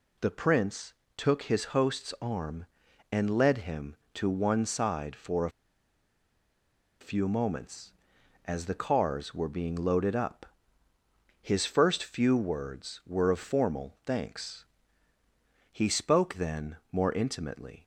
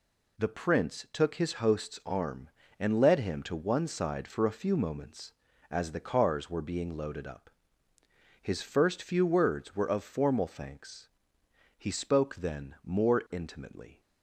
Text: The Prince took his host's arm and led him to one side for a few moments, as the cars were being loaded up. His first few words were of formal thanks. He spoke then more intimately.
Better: second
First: pauses between "Prince" and "took"; slight; at 0.9 s; 0.22 s long // pauses between "a" and "few"; strong; at 5.4 s; 1.5 s long // pauses between "then" and "more"; slight; at 16.7 s; 0.16 s long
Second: none

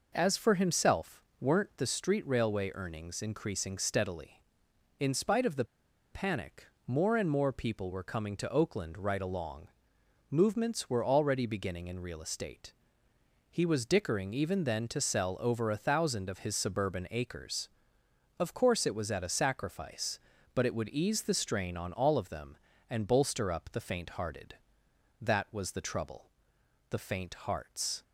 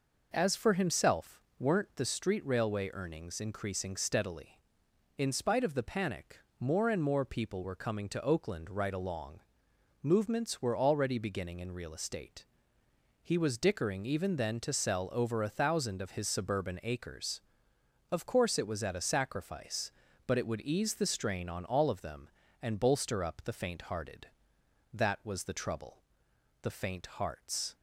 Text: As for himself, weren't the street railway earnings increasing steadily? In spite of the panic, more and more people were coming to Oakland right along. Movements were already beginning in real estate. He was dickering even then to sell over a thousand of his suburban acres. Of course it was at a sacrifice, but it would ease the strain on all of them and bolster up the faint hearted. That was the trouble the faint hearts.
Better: second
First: pauses between "the" and "panic"; noticeable; at 5.6 s; 0.48 s long // pauses between "trouble" and "the"; noticeable; at 26.2 s; 0.66 s long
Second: pauses between "trouble" and "the"; noticeable; at 25.9 s; 0.66 s long

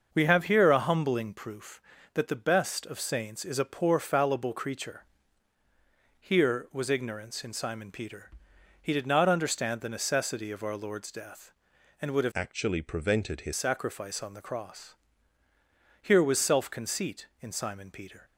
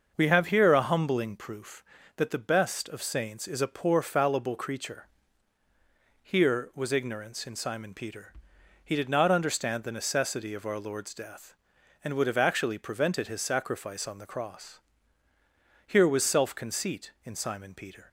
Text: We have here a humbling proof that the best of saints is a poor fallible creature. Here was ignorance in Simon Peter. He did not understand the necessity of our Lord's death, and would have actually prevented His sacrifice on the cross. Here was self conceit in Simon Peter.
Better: second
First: starts louder than the rest; noticeable; until 1.1 s; 6 dB // changes voice from "actually" to "His"; from 12.3 to 13.5 s; 1.2 s long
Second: starts louder than the rest; noticeable; until 1.1 s; 6 dB

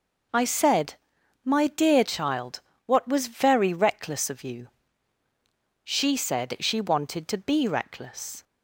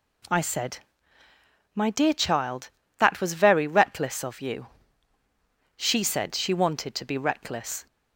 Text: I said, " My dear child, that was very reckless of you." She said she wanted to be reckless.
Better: second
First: says "what" for "that"; at 2.8 s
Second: none

